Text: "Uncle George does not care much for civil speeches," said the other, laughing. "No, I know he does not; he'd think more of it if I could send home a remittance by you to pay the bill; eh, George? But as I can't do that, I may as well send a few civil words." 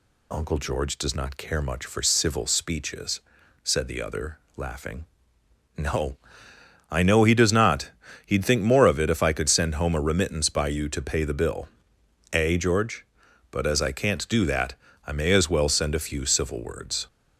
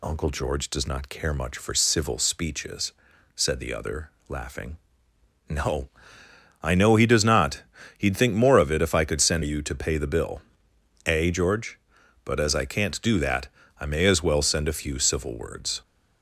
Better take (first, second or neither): first